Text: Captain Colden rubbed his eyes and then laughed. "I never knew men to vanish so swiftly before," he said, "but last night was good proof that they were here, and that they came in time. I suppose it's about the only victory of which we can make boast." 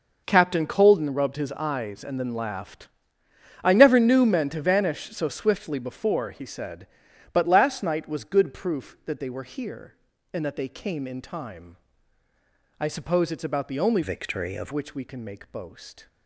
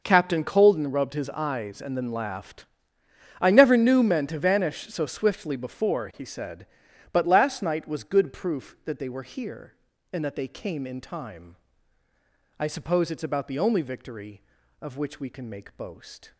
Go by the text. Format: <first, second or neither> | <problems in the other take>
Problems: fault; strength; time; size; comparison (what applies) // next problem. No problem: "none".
second | changes voice from "victory" to "of"; from 14.0 to 14.7 s; 0.7 s long